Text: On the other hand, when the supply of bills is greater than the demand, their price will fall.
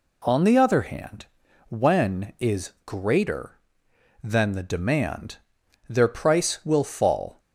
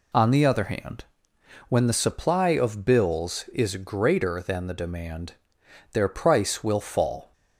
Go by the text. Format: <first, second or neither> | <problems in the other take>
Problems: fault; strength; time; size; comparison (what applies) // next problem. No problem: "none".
second | skips "the supply of bills"; at 2.3 s